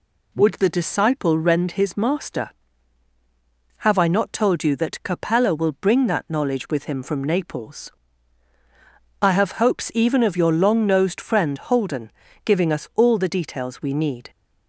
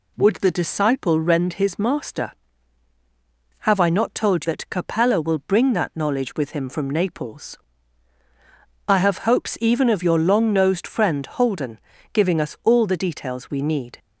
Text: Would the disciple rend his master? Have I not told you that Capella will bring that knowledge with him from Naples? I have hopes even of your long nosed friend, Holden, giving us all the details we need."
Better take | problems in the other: first | skips "you"; at 4.4 s

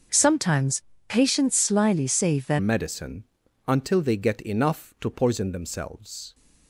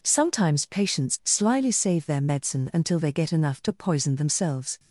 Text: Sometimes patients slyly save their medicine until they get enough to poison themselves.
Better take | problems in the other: second | starts louder than the rest; until 1.3 s; 6.5 dB // pauses between "Sometimes" and "patients"; slight; at 0.8 s; 0.24 s long // changes voice at "medicine"; from 2.5 s on; 3.8 s long // pauses between "medicine" and "until"; at 3.2 s; 0.42 s long

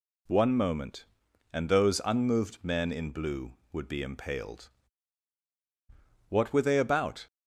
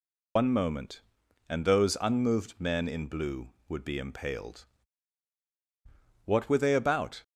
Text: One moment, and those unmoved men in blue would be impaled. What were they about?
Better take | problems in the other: first | loses the start of "One"; at 0.3 s; 130 ms

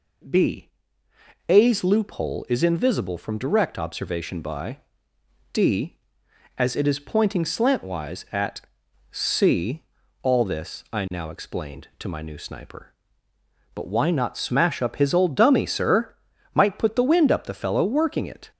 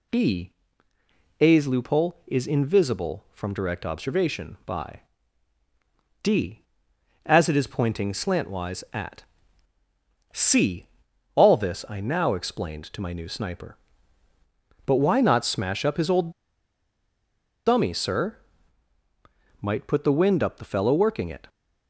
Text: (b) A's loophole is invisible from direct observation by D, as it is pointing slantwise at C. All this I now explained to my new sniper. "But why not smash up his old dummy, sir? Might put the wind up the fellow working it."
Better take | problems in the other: first | pauses between "by" and "D"; at 5.0 s; 1.2 s long; noticeable in the first // pauses between "at" and "C"; at 9.2 s; 1.0 s long; noticeable in the first // pauses between "old" and "dummy"; strong; at 16.3 s; 1.3 s long

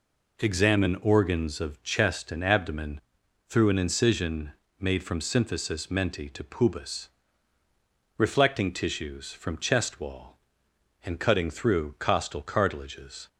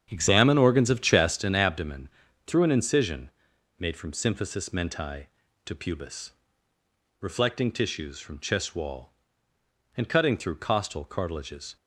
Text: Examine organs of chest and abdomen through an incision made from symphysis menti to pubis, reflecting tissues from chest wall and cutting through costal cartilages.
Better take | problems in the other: first | starts louder than the rest; strong; until 1.7 s; 8 dB // pauses between "abdomen" and "through"; at 2.0 s; 0.38 s long; noticeable in the first // pauses between "incision" and "made"; noticeable; at 3.2 s; 0.48 s long; slight in the first

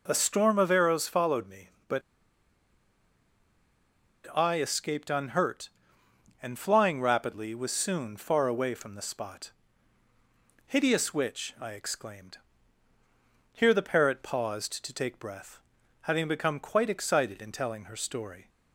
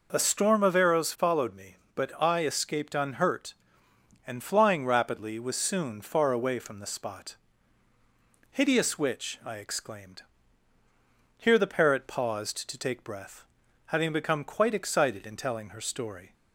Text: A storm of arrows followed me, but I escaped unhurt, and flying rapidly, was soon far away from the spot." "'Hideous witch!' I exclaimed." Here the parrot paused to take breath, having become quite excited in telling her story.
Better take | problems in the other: second | pauses between "but" and "I"; strong; at 2.0 s; 2.3 s long

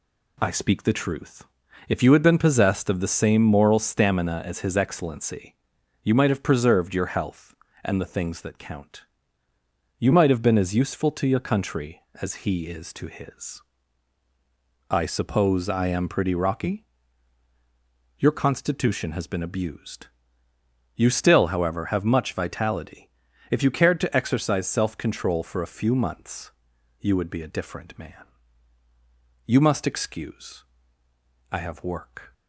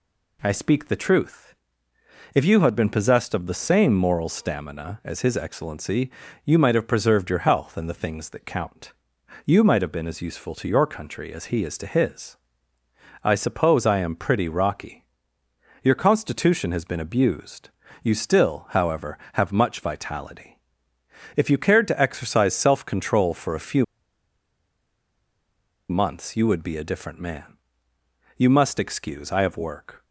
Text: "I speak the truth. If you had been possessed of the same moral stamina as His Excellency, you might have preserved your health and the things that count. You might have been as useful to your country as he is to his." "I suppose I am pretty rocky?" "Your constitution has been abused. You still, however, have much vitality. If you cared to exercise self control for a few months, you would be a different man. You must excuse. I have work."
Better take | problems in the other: first | pauses between "few" and "months"; strong; at 23.8 s; 2.0 s long

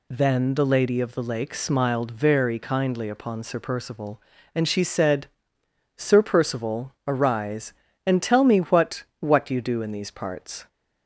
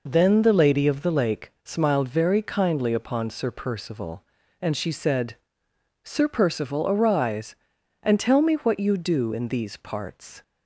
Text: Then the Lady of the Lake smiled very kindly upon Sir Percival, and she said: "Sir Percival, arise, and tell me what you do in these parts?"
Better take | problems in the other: second | says "what" twice; at 9.1 s

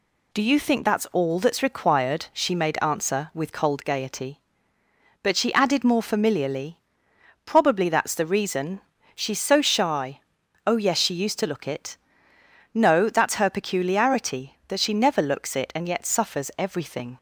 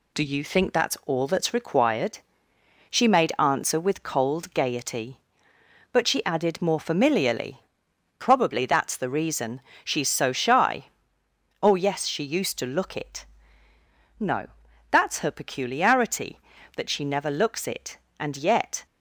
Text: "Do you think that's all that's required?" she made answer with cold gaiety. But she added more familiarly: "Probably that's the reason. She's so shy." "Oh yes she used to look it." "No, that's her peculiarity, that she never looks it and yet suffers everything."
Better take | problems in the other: first | stops before "suffers everything"; at 18.8 s

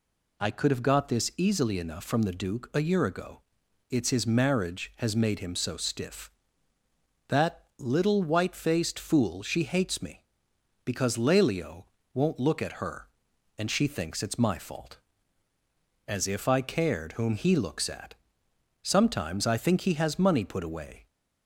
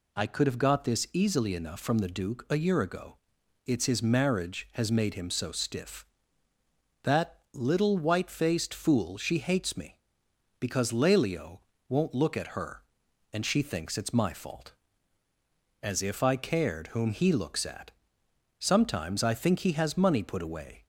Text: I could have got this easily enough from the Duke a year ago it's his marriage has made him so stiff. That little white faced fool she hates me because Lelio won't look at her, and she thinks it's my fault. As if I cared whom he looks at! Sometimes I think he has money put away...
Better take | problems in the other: neither | pauses between "ago" and "it's"; noticeable; the same in both // pauses between "Lelio" and "won't"; slight; the same in both

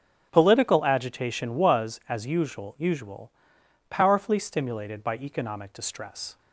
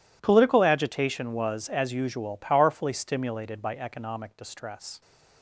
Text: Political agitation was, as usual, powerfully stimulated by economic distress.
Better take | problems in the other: second | starts louder than the rest; until 1.3 s; 6.5 dB // says "usual" twice; at 2.7 s

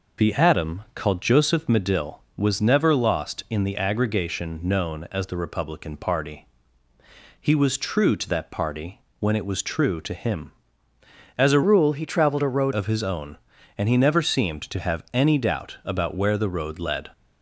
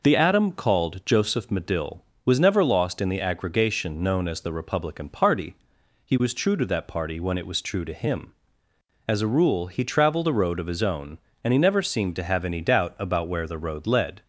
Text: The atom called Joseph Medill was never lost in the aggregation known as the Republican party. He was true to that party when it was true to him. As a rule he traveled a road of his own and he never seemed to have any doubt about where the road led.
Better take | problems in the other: second | pauses between "party" and "when"; slight; at 8.9 s; 0.22 s long // changes voice from "rule" to "road"; from 11.6 to 12.7 s; 1.1 s long

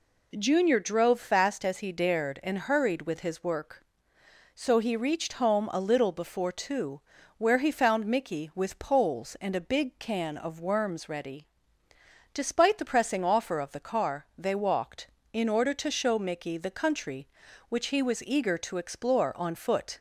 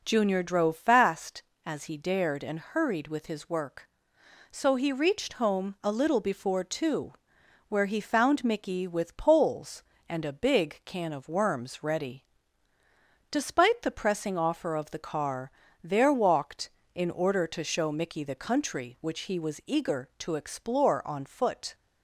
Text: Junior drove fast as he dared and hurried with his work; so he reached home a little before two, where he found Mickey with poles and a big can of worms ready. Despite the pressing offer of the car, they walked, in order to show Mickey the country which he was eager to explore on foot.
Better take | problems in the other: first | says "there" for "they"; at 15.8 s

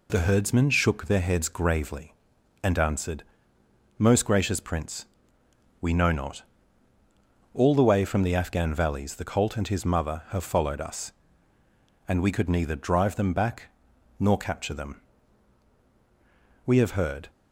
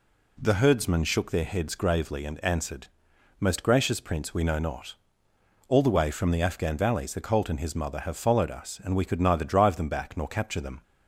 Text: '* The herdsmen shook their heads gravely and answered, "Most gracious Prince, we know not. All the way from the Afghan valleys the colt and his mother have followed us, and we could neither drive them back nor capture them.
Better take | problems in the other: second | pauses between "back" and "nor"; noticeable; at 13.6 s; 0.50 s long // goes on to say "We have heard"; noticeable; from 16.6 s on; 0.64 s long

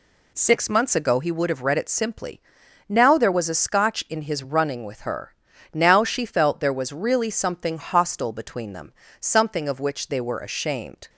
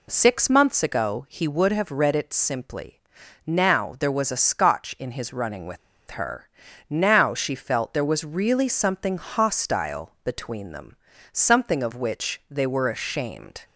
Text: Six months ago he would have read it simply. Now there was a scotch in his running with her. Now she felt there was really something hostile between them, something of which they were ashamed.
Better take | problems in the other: first | pauses between "with" and "her"; slight; at 5.7 s; 0.32 s long

